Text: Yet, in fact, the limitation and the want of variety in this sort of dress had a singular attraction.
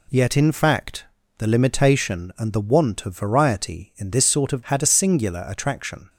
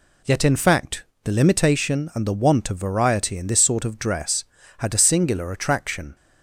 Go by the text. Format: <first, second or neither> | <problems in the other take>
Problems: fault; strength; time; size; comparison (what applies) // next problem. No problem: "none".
second | skips "dress"; at 4.6 s